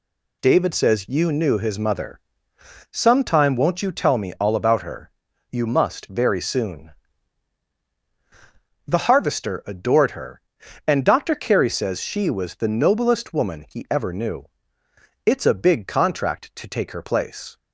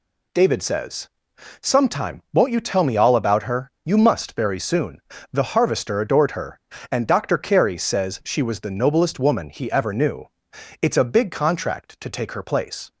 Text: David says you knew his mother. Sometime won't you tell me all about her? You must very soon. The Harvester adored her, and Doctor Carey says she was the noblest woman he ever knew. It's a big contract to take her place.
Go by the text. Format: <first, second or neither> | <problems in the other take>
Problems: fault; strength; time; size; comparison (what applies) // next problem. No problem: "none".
first | skips "you knew his mother"; at 1.3 s